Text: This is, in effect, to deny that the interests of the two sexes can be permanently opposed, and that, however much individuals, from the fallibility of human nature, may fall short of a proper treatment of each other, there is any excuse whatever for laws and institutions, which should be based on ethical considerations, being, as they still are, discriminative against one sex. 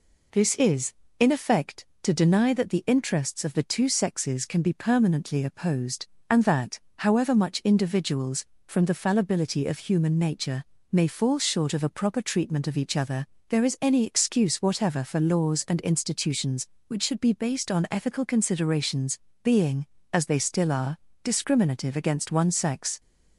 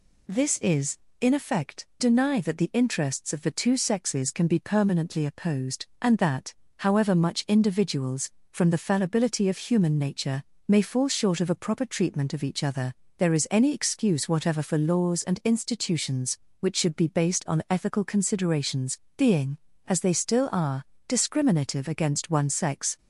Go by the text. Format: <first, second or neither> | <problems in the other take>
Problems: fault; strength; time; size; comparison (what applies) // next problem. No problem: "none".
first | skips "to"; at 1.9 s